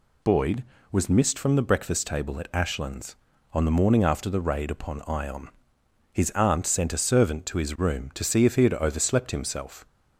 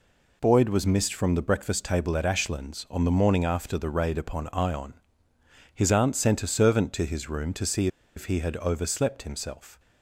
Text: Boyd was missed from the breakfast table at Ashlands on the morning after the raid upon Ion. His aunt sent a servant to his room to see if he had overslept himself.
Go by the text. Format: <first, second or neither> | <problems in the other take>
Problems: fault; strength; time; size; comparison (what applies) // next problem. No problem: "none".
first | pauses between "see" and "if"; slight; at 7.8 s; 0.29 s long